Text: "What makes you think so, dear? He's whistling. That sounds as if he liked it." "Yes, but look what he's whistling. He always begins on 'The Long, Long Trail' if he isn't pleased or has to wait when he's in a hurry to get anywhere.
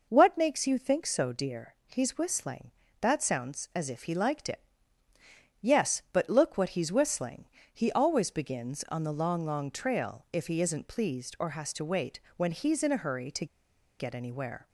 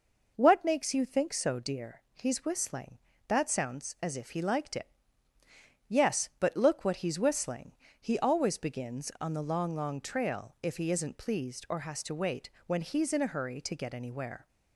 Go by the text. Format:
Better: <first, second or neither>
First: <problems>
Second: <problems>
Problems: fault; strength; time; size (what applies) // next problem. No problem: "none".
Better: second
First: pauses between "wait" and "when"; slight; at 12.1 s; 0.16 s long // pauses between "to" and "get"; noticeable; at 13.4 s; 0.53 s long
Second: pauses between "wait" and "when"; slight; at 12.4 s; 0.16 s long